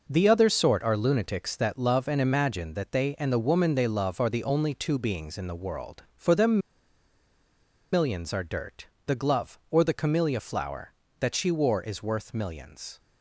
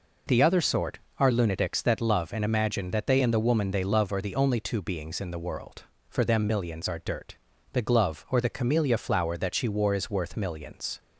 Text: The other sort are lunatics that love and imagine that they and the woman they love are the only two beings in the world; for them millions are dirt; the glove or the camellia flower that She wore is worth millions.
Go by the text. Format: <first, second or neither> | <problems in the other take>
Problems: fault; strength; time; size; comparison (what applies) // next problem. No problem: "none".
second | pauses between "them" and "millions"; strong; at 6.6 s; 1.3 s long